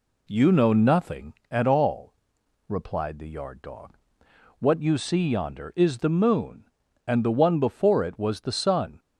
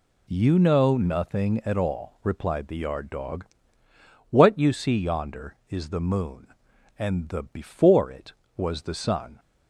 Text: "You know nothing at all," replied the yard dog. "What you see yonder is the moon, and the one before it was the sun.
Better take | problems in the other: first | skips "one"; at 7.4 s

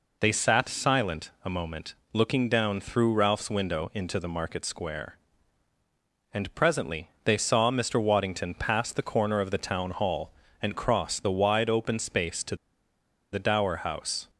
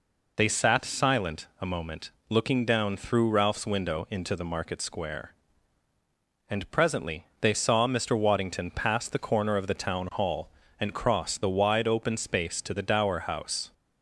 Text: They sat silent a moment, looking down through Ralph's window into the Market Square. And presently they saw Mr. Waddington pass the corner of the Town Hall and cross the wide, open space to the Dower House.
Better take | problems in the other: second | pauses between "to" and "the"; noticeable; at 12.5 s; 0.77 s long

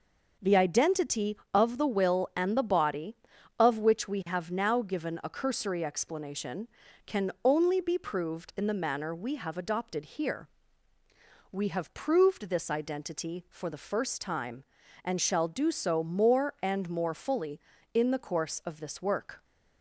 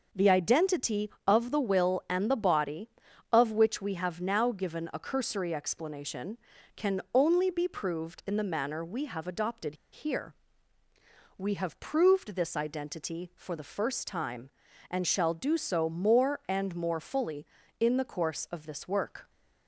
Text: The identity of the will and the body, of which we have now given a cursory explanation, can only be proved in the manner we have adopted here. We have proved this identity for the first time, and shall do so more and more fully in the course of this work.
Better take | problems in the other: first | pauses between "adopted" and "here"; slight; at 9.7 s; 0.17 s long

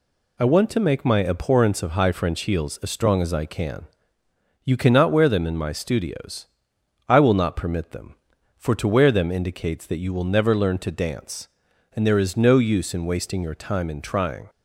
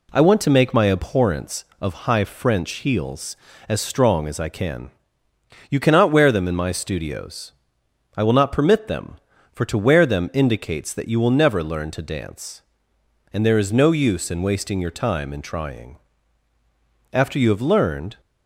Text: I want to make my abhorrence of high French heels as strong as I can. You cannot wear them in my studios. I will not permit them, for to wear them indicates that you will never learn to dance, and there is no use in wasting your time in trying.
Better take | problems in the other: first | goes on to say "After you have learned"; noticeable; from 17.1 s on; 1.0 s long

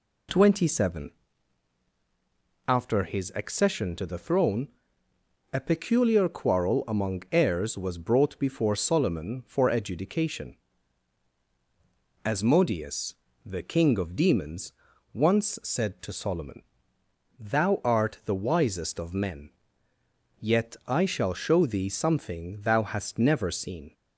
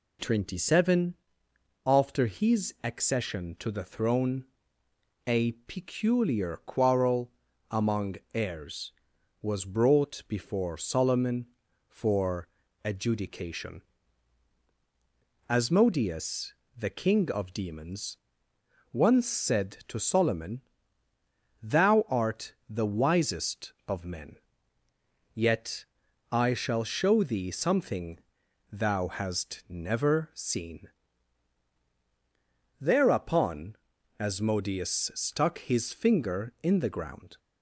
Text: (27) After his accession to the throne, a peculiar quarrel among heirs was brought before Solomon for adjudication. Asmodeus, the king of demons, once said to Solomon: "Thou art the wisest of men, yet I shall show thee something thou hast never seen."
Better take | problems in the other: first | pauses between "quarrel" and "among"; at 7.3 s; 0.40 s long // pauses between "among" and "heirs"; slight; at 8.1 s; 0.18 s long // pauses between "for" and "adjudication"; slight; at 12.4 s; 0.36 s long // pauses between "art" and "the"; slight; at 22.5 s; 0.16 s long // pauses between "yet" and "I"; at 25.8 s; 0.44 s long // pauses between "something" and "thou"; noticeable; at 28.2 s; 0.50 s long // goes on to say "Thereupon Asmodeus stuck his finger in the ground"; strong; from 32.8 s on; 4.5 s long

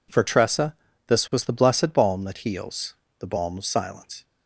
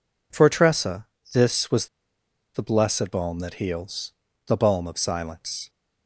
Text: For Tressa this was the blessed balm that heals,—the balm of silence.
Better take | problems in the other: first | pauses between "Tressa" and "this"; slight; at 1.0 s; 0.28 s long; slight in the first // pauses between "was" and "the"; noticeable; at 1.8 s; 0.67 s long

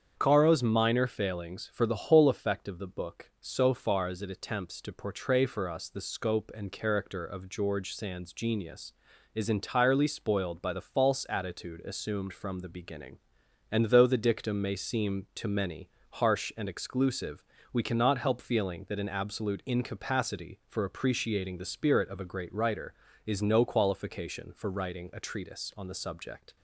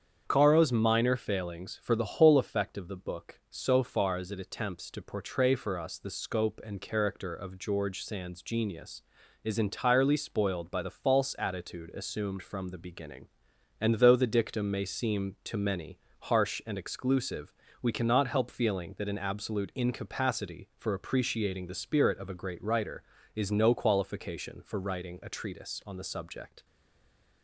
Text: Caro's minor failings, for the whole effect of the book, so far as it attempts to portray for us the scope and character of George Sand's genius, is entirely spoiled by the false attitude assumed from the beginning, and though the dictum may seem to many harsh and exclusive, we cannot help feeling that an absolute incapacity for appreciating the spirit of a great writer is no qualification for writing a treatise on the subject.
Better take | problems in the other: first | starts louder than the rest; strong; until 1.2 s; 7.5 dB; strong in the first // pauses between "many" and "harsh"; slight; at 15.9 s; 0.22 s long; slight in the first // stays silent after the last word; slight; from 26.6 s on; 0.8 s long

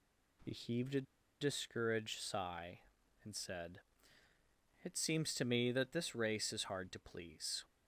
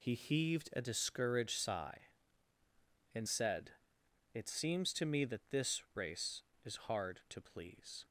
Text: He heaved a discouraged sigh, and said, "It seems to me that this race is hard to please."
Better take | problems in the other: second | pauses between "a" and "discouraged"; at 1.0 s; 0.40 s long

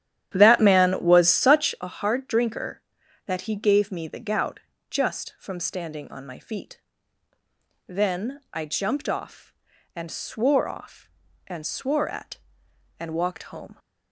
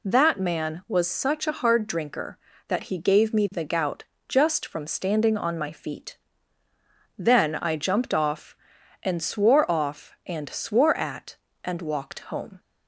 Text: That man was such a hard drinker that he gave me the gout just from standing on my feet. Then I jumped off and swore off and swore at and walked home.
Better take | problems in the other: second | starts louder than the rest; strong; until 1.9 s; 11 dB // pauses between "gout" and "just"; slight; at 4.6 s; 0.28 s long; slight in the second

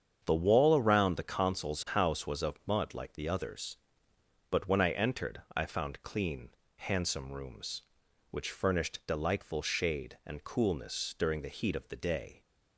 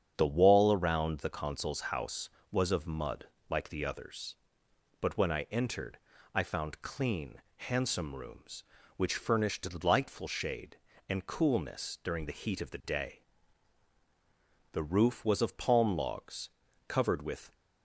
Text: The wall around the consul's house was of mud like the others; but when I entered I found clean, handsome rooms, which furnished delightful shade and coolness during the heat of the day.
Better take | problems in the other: first | starts louder than the rest; strong; until 1.1 s; 8 dB; strong in the first // pauses between "mud" and "like"; slight; at 3.2 s; 0.24 s long // pauses between "entered" and "I"; slight; at 5.9 s; 0.36 s long // goes on to say "The roof was of palm logs covered with"; strong; from 14.7 s on; 2.8 s long

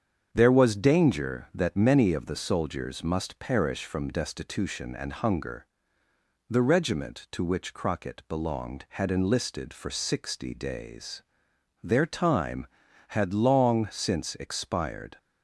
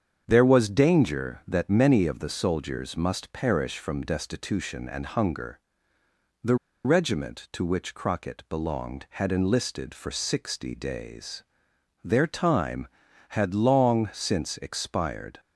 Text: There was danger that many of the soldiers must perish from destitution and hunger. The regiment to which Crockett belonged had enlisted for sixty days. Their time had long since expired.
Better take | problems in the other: first | starts louder than the rest; strong; until 1.2 s; 7.5 dB; strong in the first // pauses between "The" and "regiment"; slight; at 6.5 s; 0.29 s long

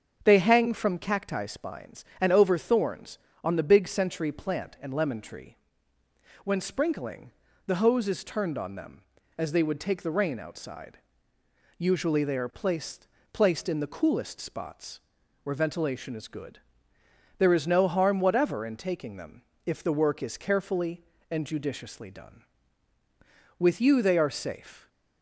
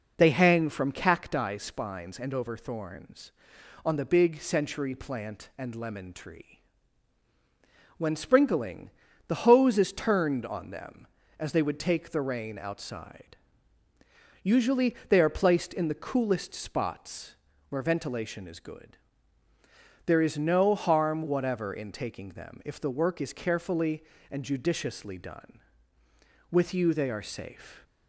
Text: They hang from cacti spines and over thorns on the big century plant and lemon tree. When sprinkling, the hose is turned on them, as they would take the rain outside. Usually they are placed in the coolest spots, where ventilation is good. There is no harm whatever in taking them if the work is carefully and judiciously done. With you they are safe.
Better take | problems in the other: second | starts louder than the rest; until 1.2 s; 6.5 dB // says "placed" twice; at 13.3 s // pauses between "them" and "if"; slight; at 19.4 s; 0.24 s long

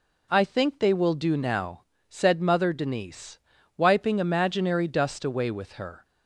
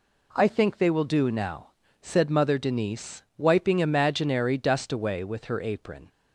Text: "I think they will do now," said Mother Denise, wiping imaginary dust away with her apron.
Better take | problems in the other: second | stops before "apron"; at 6.0 s

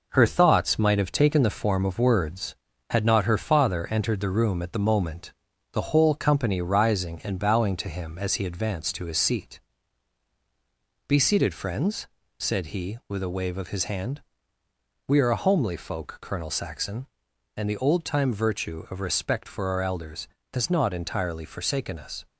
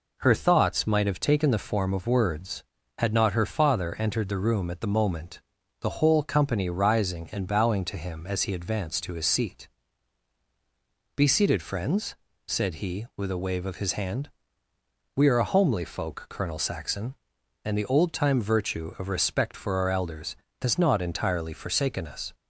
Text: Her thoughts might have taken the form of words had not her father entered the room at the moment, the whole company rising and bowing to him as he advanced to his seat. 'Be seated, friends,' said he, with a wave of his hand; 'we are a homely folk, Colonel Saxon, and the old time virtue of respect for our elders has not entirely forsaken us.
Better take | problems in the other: second | gets quieter; noticeable; throughout; 4.5 dB

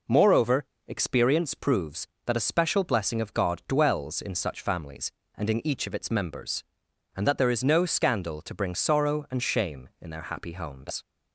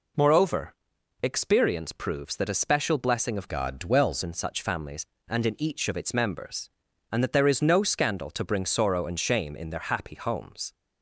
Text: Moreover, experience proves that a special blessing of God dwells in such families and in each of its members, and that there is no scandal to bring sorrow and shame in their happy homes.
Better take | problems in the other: first | changes voice from "God" to "dwells"; from 3.4 to 4.2 s; 0.8 s long

